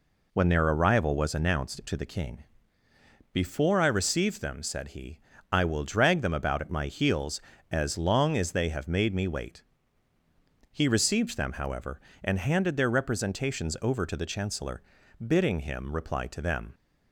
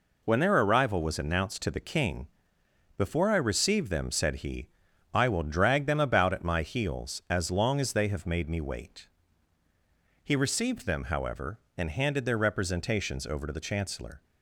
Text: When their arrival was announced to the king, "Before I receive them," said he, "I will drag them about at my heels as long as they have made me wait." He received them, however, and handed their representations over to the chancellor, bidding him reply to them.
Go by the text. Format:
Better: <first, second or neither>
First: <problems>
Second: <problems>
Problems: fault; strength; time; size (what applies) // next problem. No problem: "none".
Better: first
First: none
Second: stops before "bidding him reply to them"; at 14.2 s